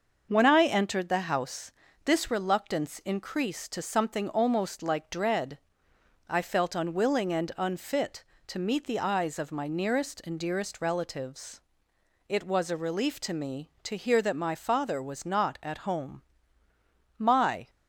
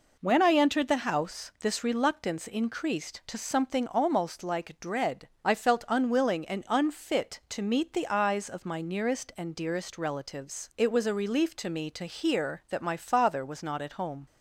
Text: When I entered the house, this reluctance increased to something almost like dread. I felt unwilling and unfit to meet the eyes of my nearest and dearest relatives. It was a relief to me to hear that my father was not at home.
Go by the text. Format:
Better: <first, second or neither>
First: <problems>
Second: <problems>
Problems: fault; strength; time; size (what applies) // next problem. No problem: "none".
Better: second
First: starts louder than the rest; until 1.3 s; 6 dB // goes on to say "My"; from 17.1 s on; 0.52 s long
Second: none